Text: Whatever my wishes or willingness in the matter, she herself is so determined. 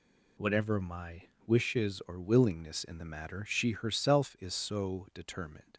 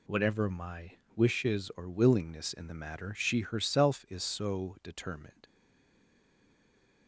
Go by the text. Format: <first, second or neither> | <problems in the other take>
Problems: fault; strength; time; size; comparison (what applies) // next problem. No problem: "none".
first | pauses between "my" and "wishes"; slight; at 0.9 s; 0.24 s long; slight in the first // stays silent after the last word; noticeable; from 5.4 s on; 1.6 s long